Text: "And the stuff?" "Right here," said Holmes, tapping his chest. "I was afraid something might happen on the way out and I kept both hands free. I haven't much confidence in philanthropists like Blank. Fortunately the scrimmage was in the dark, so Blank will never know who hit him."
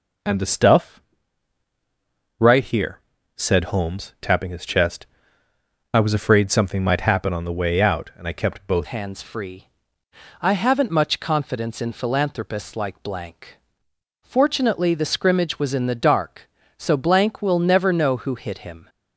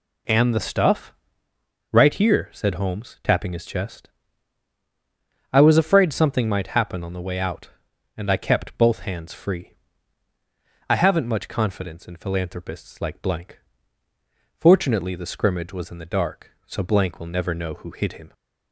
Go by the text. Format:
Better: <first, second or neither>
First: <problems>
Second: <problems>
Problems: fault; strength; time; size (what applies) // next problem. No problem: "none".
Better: second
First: changes voice at "hands"; from 8.8 s on; 10.0 s long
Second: none